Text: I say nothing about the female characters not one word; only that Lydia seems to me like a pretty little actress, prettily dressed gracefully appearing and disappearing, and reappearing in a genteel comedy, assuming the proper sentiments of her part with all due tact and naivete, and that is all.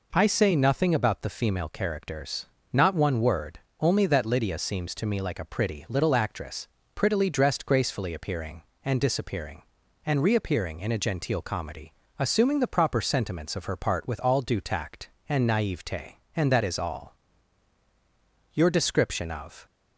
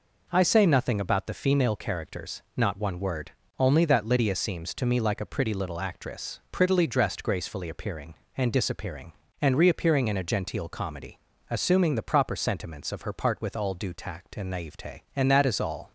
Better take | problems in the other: second | pauses between "characters" and "not"; slight; at 2.4 s; 0.28 s long; slight in the second // goes on to say "Your description of"; noticeable; from 18.5 s on; 1.1 s long

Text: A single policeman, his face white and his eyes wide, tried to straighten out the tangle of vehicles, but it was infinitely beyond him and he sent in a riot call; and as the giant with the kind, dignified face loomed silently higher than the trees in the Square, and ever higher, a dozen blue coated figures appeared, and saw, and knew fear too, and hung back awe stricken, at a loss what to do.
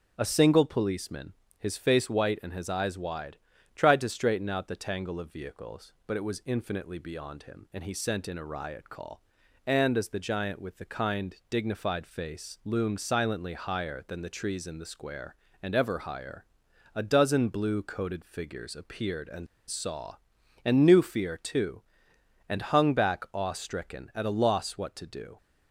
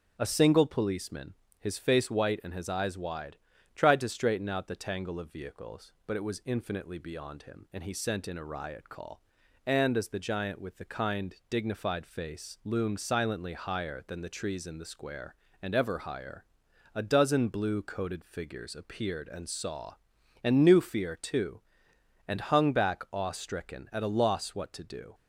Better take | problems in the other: second | pauses between "and" and "saw"; slight; at 19.4 s; 0.22 s long

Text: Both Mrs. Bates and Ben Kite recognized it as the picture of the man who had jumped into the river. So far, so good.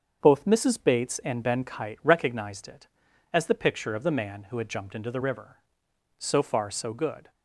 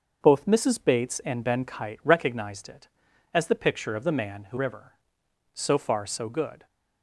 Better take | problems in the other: first | starts louder than the rest; until 1.2 s; 6.5 dB; also in the first // skips "had jumped into the"; at 4.5 s

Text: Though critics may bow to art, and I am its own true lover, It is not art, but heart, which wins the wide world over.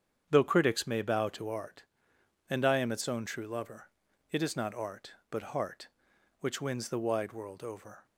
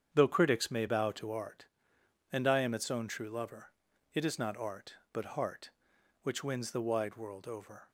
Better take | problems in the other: neither | starts louder than the rest; strong; the same in both

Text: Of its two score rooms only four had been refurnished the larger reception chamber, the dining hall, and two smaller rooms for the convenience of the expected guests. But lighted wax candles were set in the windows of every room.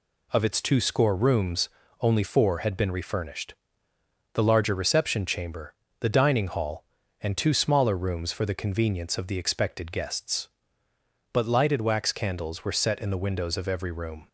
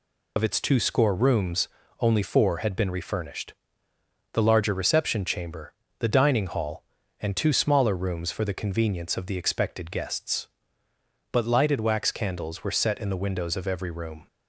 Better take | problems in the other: first | loses the start of "Of"; at 0.3 s; 65 ms // pauses between "rooms" and "only"; slight; at 1.6 s; 0.32 s long; slight in the first // pauses between "refurnished" and "the"; noticeable; at 3.5 s; 0.80 s long; noticeable in the first

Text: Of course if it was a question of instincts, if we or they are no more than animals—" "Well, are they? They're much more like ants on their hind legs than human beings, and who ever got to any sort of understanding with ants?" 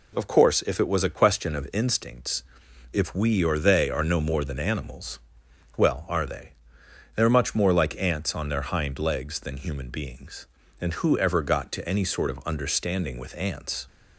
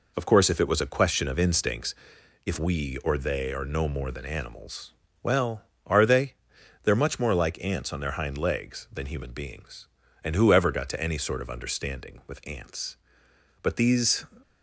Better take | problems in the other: first | goes on to say "But these"; noticeable; from 13.6 s on; 0.64 s long

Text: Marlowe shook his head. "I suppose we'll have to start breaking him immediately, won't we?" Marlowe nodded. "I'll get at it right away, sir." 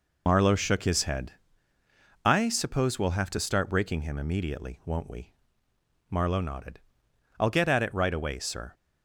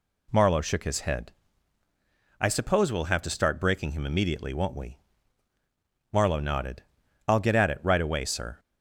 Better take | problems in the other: second | loses the start of "Marlowe"; at 0.2 s; 65 ms

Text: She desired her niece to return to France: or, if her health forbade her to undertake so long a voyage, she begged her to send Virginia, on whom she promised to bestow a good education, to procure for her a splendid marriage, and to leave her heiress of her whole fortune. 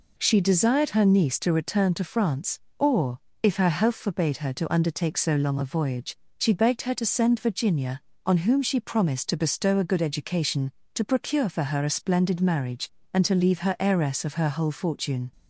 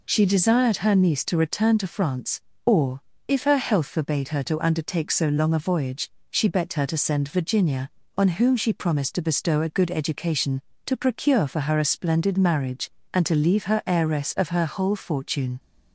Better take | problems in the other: neither | none

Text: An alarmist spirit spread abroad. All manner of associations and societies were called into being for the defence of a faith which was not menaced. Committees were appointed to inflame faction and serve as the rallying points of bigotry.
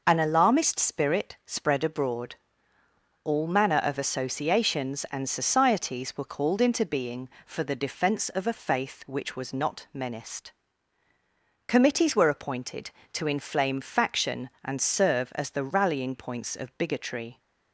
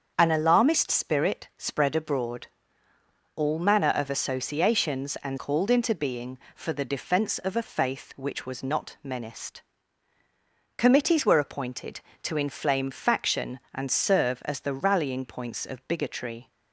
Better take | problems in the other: first | starts louder than the rest; until 1.1 s; 7 dB // skips "societies were"; at 5.3 s

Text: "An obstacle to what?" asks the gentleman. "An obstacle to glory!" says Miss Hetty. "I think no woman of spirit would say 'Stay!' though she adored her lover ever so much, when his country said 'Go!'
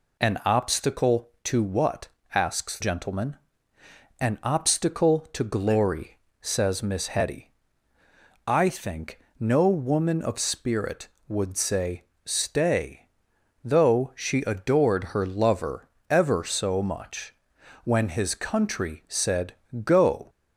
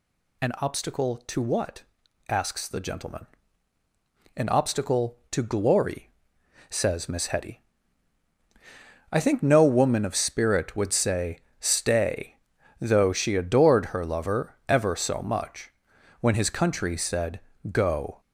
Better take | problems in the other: second | skips "the"; at 2.7 s // pauses between "think" and "no"; slight; at 9.1 s; 0.20 s long // pauses between "say" and "Stay"; slight; at 12.0 s; 0.20 s long; slight in the second // pauses between "lover" and "ever"; slight; at 15.8 s; 0.22 s long // pauses between "said" and "Go"; slight; at 19.5 s; 0.30 s long; slight in the second

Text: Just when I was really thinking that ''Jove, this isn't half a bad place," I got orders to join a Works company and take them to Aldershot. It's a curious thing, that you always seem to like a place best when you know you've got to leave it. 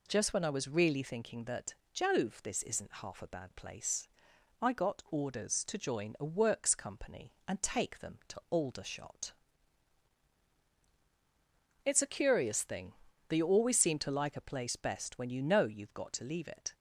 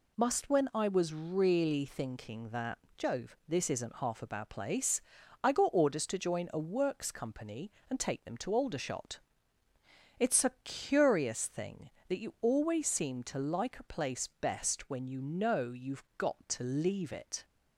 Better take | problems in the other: first | says "Must" for "Just"; at 0.1 s // pauses between "that" and "Jove"; slight; at 2.7 s; 0.18 s long; slight in the first

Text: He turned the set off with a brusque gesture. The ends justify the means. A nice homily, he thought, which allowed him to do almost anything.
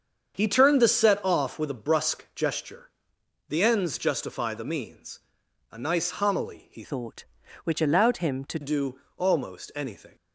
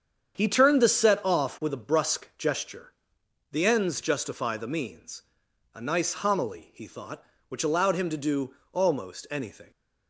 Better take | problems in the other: second | starts louder than the rest; strong; until 1.3 s; 7 dB; strong in the second // changes voice from "thought" to "to"; from 6.8 to 8.5 s; 1.7 s long // pauses between "do" and "almost"; slight; at 8.9 s; 0.18 s long; slight in the second

